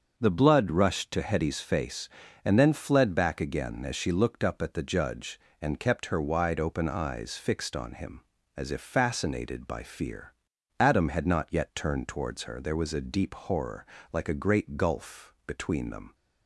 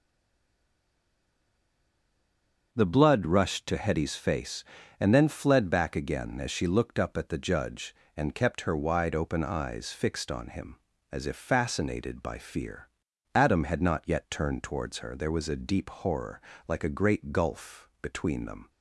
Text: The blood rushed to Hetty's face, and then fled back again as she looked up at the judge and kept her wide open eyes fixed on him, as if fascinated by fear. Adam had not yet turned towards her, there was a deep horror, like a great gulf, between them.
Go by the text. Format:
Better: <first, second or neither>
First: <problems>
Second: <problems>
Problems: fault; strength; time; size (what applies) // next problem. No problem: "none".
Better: first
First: starts louder than the rest; until 1.1 s; 6 dB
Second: stays silent before the first word; strong; until 2.7 s; 2.7 s long // starts louder than the rest; until 3.7 s; 6 dB